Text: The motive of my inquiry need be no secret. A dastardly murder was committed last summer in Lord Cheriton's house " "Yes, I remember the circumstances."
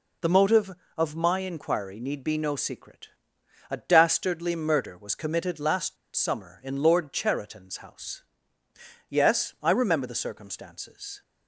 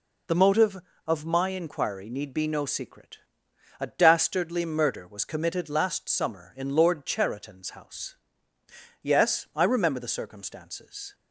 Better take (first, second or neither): second